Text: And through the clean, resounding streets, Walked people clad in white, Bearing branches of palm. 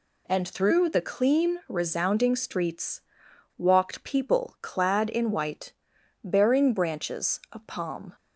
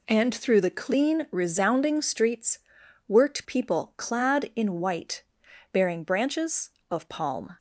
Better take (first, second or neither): first